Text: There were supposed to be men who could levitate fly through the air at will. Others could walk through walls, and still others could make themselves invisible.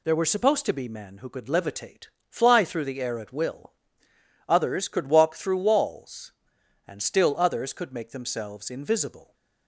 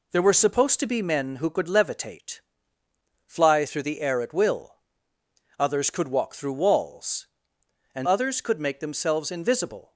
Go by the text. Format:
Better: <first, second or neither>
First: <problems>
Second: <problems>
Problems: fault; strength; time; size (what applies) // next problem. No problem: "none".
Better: first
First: pauses between "levitate" and "fly"; slight; at 2.0 s; 0.22 s long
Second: pauses between "levitate" and "fly"; noticeable; at 2.3 s; 0.88 s long // skips "still"; at 8.0 s